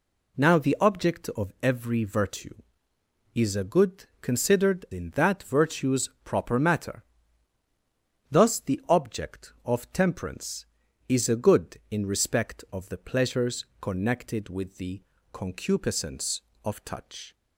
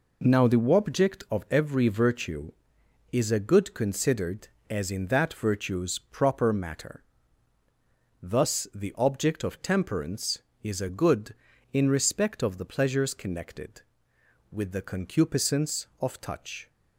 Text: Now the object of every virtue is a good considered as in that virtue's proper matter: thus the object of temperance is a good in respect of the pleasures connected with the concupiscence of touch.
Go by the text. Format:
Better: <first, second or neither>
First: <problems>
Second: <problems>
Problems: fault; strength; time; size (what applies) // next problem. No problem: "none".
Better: second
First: pauses between "good" and "considered"; slight; at 4.0 s; 0.16 s long // skips "as"; at 4.8 s // pauses between "pleasures" and "connected"; slight; at 13.6 s; 0.16 s long // pauses between "the" and "concupiscence"; slight; at 15.0 s; 0.30 s long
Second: none